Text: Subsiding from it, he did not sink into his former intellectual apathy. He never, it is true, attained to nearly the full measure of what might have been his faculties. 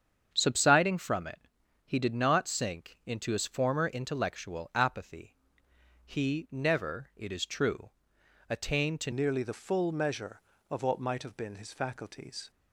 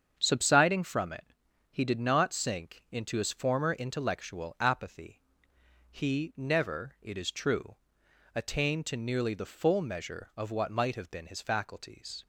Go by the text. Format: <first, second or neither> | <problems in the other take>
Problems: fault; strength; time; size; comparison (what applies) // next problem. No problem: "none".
second | starts louder than the rest; strong; until 1.3 s; 7.5 dB; strong in the second // changes voice at "nearly"; from 9.1 s on; 3.4 s long